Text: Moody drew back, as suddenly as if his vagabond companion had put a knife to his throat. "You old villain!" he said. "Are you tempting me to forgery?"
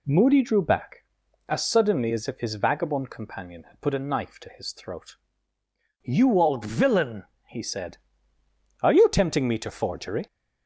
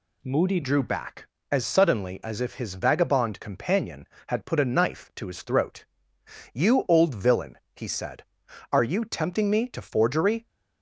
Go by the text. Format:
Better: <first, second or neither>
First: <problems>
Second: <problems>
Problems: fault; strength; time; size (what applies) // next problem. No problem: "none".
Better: first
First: none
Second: changes voice at "drew"; from 0.6 s on; 9.8 s long